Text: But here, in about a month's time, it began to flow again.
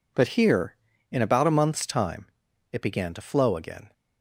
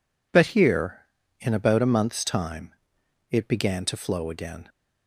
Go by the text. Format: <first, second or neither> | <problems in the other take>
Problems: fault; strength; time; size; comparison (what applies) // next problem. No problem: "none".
neither | none